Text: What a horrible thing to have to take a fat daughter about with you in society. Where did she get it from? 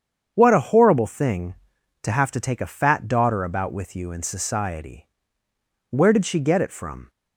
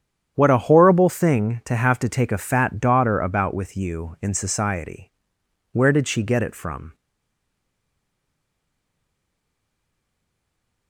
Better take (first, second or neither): first